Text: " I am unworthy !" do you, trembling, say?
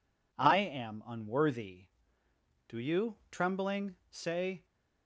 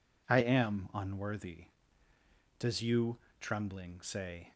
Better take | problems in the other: first | says "does" for "do"; at 2.5 s

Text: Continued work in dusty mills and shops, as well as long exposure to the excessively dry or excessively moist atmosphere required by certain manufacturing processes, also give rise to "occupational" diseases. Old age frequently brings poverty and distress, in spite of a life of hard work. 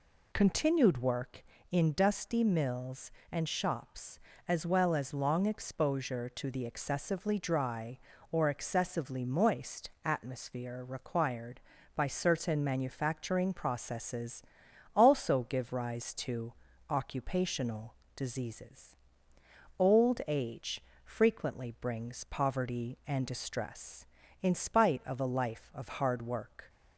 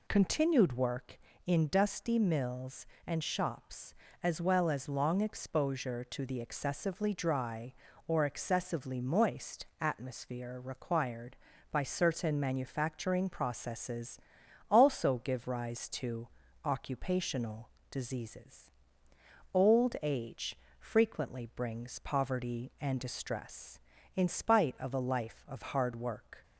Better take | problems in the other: neither | pauses between "moist" and "atmosphere"; slight; the same in both // pauses between "to" and "occupational"; slight; the same in both // pauses between "occupational" and "diseases"; slight; the same in both // pauses between "age" and "frequently"; slight; the same in both

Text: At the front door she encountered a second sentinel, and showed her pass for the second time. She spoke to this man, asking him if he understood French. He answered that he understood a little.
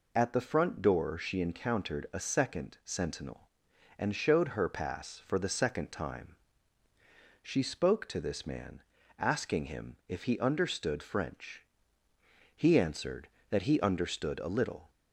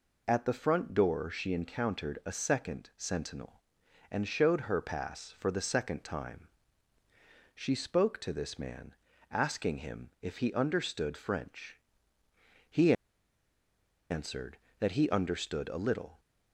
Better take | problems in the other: first | pauses between "He" and "answered"; at 12.9 s; 1.1 s long

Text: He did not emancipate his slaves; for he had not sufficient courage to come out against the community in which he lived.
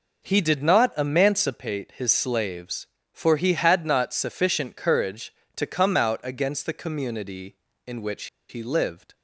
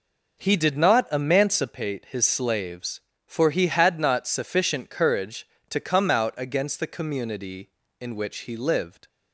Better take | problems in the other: second | pauses between "which" and "he"; slight; at 8.2 s; 0.22 s long

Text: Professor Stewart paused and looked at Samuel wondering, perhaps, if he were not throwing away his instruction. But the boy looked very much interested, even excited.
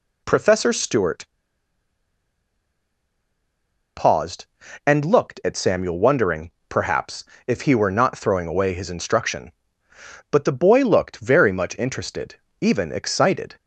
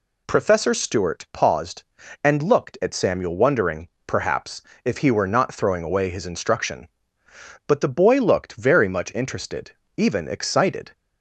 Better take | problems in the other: second | pauses between "Stewart" and "paused"; strong; at 1.2 s; 2.7 s long

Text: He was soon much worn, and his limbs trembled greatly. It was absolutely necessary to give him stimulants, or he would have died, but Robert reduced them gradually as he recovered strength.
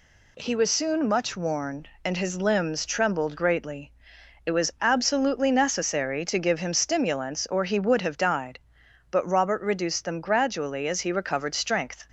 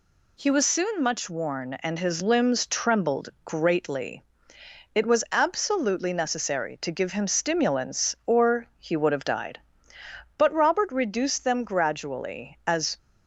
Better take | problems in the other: first | stops before "he recovered strength"; at 12.9 s

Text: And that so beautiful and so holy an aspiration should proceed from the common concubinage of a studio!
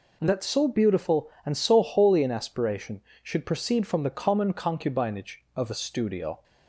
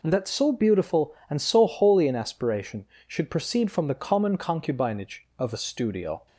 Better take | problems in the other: neither | none

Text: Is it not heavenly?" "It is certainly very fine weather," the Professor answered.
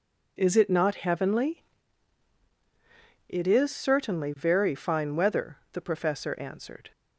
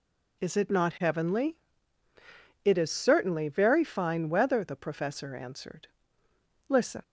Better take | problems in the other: first | goes on to say "Listen"; slight; from 6.6 s on; 0.34 s long

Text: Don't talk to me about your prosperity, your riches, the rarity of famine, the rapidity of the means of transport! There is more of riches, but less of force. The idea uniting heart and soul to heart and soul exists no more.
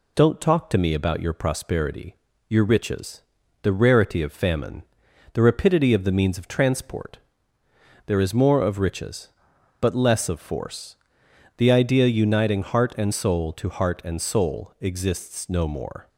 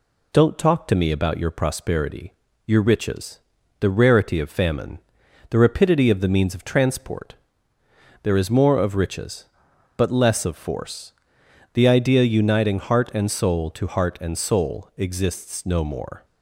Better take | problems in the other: neither | none

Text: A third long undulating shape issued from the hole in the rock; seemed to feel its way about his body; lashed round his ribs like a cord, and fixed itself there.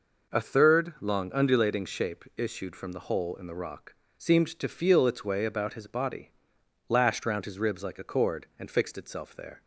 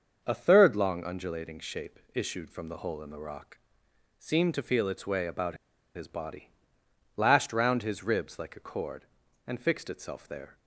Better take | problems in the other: first | starts louder than the rest; until 1.2 s; 6.5 dB // pauses between "shape" and "issued"; slight; at 1.9 s; 0.16 s long // pauses between "about" and "his"; at 5.5 s; 0.38 s long

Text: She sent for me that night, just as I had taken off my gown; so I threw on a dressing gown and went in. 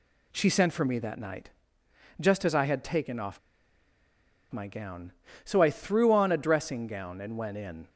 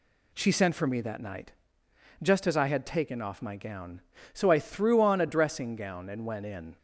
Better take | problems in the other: second | pauses between "off" and "my"; at 3.3 s; 1.1 s long

